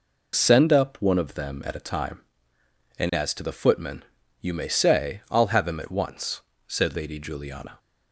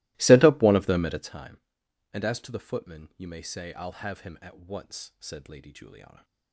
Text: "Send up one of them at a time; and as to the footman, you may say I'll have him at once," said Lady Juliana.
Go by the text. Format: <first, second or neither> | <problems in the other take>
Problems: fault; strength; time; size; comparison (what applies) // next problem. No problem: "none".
first | starts louder than the rest; strong; until 1.4 s; 20 dB